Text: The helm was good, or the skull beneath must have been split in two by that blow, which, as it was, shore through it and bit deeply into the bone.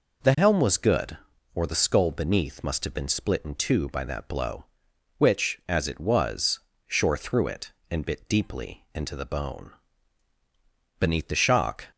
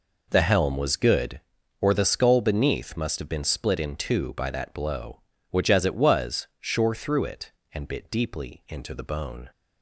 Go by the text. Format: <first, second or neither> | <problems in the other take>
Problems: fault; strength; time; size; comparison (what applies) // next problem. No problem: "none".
second | goes on to say "Beneath the shock"; noticeable; from 10.9 s on; 0.88 s long